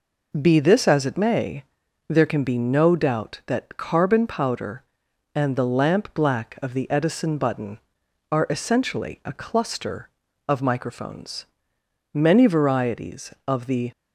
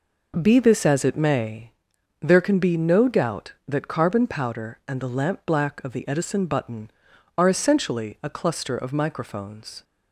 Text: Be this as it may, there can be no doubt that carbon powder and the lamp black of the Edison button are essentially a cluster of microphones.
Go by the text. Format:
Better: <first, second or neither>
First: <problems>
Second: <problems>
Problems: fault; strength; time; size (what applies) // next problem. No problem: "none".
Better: second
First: goes on to say "Many varieties of the"; strong; from 12.1 s on; 1.7 s long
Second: none